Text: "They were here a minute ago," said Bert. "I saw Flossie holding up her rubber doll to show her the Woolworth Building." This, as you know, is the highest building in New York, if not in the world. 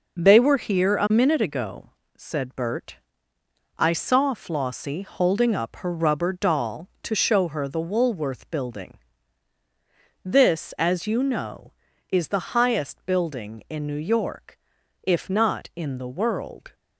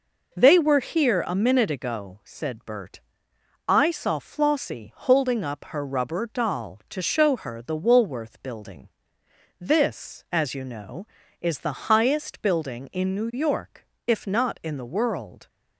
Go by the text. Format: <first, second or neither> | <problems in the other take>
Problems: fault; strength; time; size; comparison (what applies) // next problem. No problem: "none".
neither | none